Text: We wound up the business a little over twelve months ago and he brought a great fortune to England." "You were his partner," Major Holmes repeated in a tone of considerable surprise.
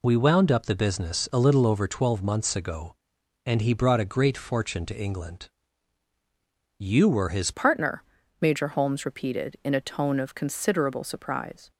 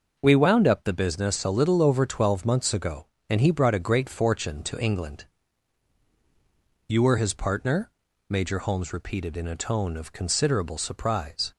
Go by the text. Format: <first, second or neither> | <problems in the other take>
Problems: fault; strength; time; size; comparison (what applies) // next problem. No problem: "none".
second | changes voice at "partner"; from 7.5 s on; 4.2 s long